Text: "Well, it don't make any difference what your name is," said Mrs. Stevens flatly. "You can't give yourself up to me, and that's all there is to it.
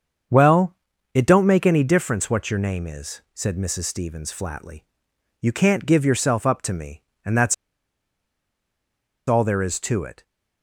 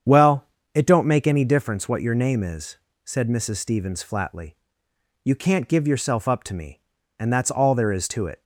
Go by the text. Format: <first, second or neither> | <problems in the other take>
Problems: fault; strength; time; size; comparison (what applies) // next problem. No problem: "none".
second | starts louder than the rest; until 1.6 s; 7 dB; strong in the second // pauses between "that's" and "all"; strong; at 7.5 s; 1.7 s long